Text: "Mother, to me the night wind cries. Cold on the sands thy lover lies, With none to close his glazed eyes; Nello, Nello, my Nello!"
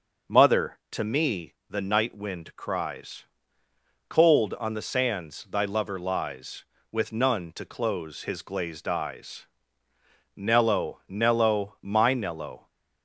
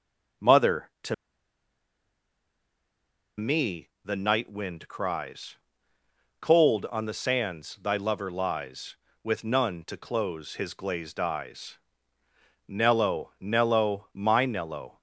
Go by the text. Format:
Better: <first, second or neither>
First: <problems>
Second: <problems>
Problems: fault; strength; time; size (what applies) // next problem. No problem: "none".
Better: first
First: pauses between "me" and "the"; slight; at 1.5 s; 0.16 s long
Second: pauses between "to" and "me"; strong; at 1.1 s; 2.2 s long // pauses between "me" and "the"; slight; at 3.8 s; 0.16 s long